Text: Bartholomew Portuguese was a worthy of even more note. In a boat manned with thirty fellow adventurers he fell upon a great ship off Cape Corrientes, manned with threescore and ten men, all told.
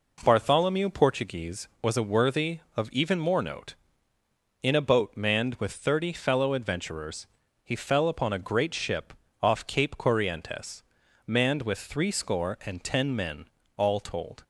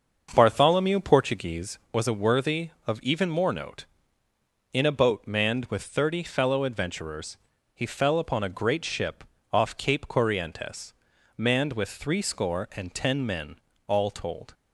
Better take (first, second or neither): first